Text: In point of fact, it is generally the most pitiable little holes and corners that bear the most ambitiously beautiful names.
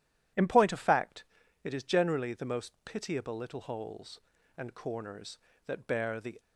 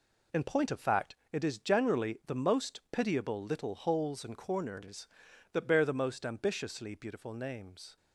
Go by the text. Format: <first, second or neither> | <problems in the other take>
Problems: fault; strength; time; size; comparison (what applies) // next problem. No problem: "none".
second | stops before "most ambitiously beautiful names"; at 6.3 s